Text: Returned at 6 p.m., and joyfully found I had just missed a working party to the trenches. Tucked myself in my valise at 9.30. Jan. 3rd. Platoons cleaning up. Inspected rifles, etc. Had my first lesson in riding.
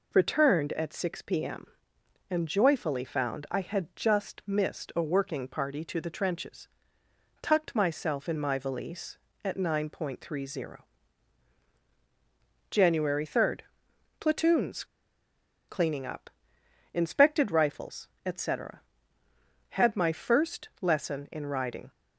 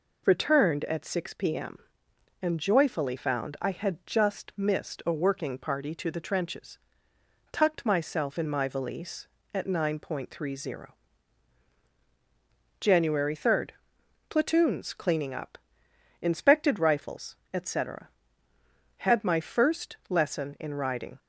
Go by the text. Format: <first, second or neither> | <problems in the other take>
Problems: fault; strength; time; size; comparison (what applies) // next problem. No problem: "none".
second | pauses between "Platoons" and "cleaning"; noticeable; at 14.8 s; 0.84 s long